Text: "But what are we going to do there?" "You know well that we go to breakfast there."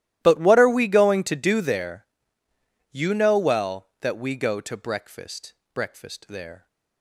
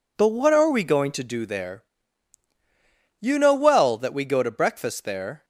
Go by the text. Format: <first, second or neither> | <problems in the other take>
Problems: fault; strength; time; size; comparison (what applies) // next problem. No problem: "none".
second | starts louder than the rest; strong; until 1.2 s; 14 dB // says "breakfast" twice; at 5.7 s